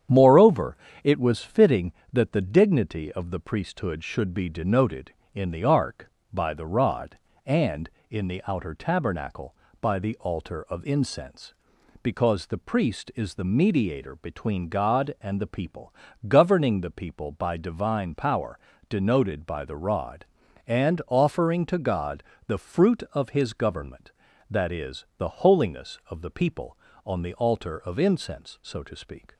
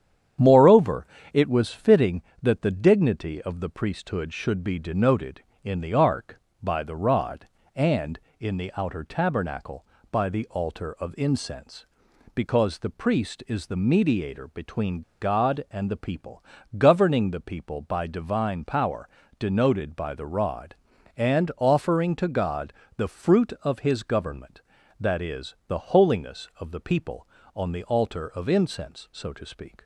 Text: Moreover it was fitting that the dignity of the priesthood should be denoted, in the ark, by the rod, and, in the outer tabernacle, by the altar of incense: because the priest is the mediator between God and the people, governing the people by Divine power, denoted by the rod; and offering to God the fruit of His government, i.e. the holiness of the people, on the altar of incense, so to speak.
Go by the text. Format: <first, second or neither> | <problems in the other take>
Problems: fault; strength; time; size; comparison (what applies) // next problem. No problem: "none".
first | starts louder than the rest; strong; until 1.7 s; 9 dB; strong in the first // pauses between "Moreover" and "it"; slight; at 1.0 s; 0.28 s long; slight in the first // pauses between "between" and "God"; slight; at 15.0 s; 0.20 s long // pauses between "God" and "the"; slight; at 22.7 s; 0.22 s long; slight in the first